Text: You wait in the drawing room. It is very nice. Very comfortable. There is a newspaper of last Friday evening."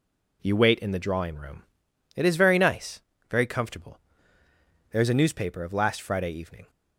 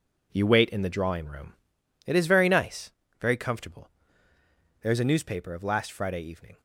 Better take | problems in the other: first | gets quieter; strong; throughout; 9.5 dB

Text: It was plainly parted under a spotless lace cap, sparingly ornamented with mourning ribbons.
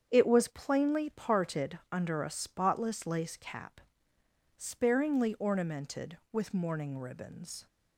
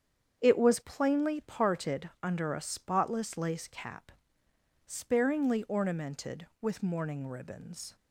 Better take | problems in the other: neither | starts louder than the rest; strong; the same in both

